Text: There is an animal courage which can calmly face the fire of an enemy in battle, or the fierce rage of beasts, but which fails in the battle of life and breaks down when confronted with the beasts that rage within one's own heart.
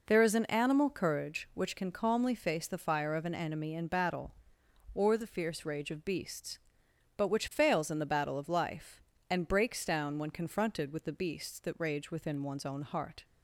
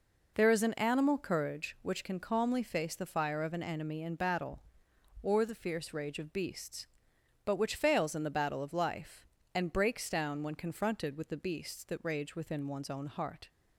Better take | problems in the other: neither | none

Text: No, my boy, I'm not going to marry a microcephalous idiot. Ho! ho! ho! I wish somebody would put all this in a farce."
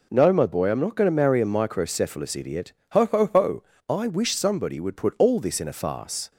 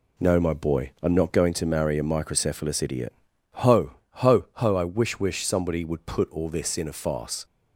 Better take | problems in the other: first | says "wish" twice; at 5.1 s

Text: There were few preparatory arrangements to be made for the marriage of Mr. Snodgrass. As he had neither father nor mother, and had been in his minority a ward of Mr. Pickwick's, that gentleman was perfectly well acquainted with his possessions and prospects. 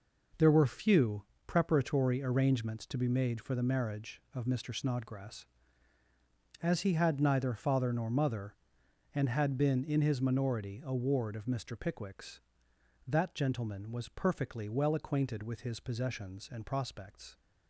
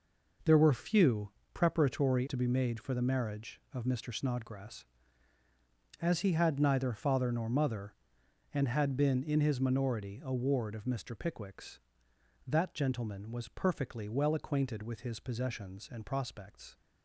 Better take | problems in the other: first | pauses between "few" and "preparatory"; slight; at 1.3 s; 0.22 s long; slight in the first // skips "arrangements"; at 2.2 s

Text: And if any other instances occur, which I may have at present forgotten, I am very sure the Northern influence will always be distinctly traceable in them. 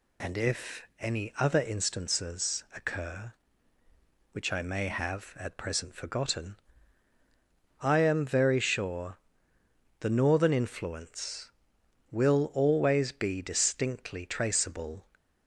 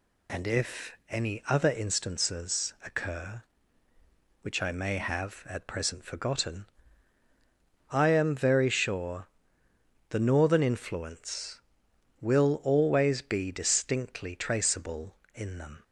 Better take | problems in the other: second | pauses between "if" and "any"; slight; at 0.8 s; 0.16 s long; slight in the second // pauses between "sure" and "the"; noticeable; at 9.1 s; 0.84 s long; noticeable in the second // stops before "in them"; at 15.1 s

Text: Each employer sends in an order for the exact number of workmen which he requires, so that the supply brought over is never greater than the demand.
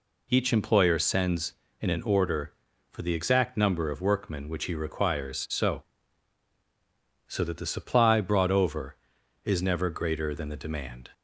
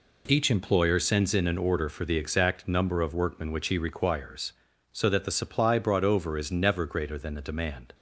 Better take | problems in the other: second | says "so" twice; at 7.2 s

